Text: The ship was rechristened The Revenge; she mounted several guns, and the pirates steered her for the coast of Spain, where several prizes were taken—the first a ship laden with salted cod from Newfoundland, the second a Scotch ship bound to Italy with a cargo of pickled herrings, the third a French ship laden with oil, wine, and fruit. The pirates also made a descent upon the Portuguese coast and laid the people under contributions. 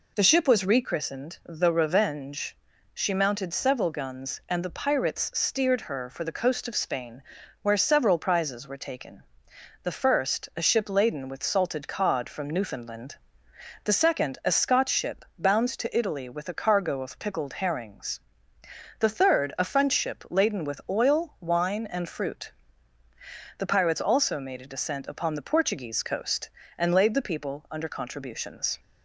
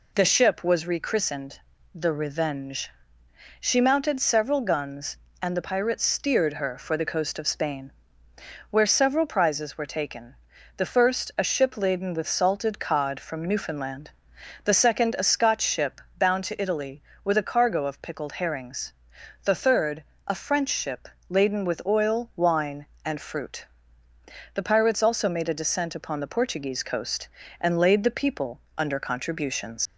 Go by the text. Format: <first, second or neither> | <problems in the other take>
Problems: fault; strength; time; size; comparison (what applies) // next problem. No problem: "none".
first | pauses between "rechristened" and "The"; slight; at 1.6 s; 0.34 s long // pauses between "ship" and "bound"; slight; at 16.0 s; 0.16 s long // pauses between "third" and "a"; slight; at 20.0 s; 0.22 s long // pauses between "ship" and "laden"; slight; at 21.0 s; 0.22 s long // pauses between "people" and "under"; slight; at 28.5 s; 0.20 s long // leaves "contributions" unfinished; at 29.8 s; 80 ms